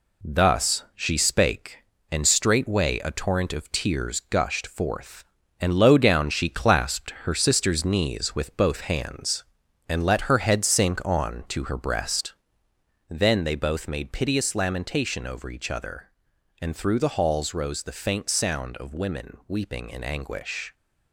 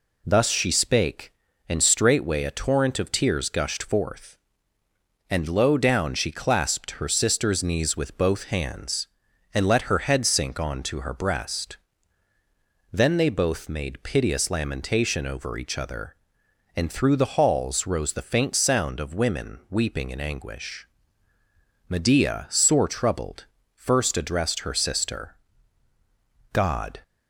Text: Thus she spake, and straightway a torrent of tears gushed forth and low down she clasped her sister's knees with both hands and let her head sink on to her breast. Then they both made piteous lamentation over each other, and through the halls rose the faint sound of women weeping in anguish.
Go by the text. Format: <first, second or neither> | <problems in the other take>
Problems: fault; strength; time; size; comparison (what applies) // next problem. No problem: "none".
first | goes on to say "Medea sore troubled first addressed her sister God"; strong; from 21.8 s on; 5.1 s long